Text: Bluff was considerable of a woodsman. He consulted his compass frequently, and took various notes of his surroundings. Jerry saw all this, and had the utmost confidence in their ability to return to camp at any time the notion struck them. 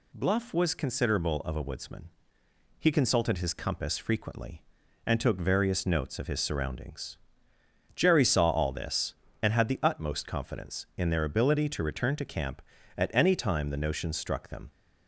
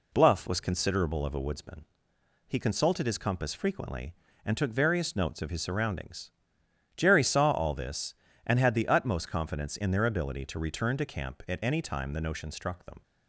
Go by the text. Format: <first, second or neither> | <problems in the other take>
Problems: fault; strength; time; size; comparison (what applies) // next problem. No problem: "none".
neither | none